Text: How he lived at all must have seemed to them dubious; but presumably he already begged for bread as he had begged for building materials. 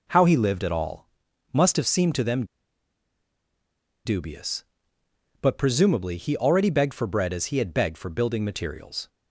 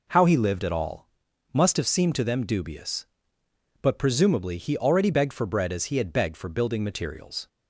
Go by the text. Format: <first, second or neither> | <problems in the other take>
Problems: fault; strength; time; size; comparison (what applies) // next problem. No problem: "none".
second | pauses between "all" and "must"; noticeable; at 1.0 s; 0.46 s long; noticeable in the second // pauses between "them" and "dubious"; strong; at 2.4 s; 1.5 s long